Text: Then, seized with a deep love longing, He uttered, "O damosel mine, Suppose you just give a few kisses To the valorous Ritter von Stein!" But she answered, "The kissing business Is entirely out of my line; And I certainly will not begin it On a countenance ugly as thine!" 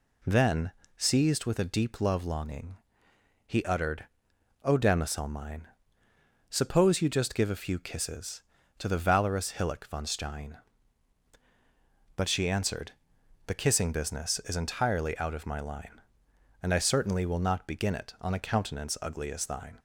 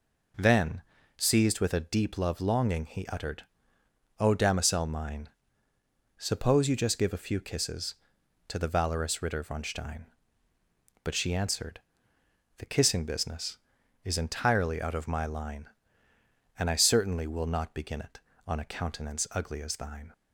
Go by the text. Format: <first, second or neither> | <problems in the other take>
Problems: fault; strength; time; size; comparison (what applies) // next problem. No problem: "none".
second | says "Hillock" for "Ritter"; at 9.5 s